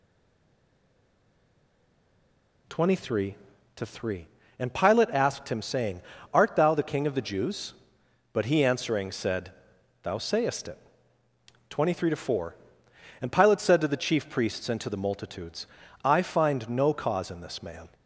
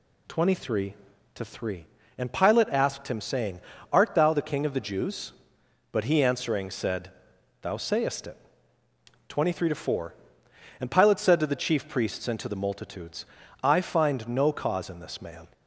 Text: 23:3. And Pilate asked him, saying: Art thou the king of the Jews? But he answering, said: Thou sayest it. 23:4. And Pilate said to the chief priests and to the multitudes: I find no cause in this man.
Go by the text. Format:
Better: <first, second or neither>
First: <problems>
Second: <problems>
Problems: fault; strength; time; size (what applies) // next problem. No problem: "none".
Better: second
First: stays silent before the first word; strong; until 2.6 s; 2.6 s long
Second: none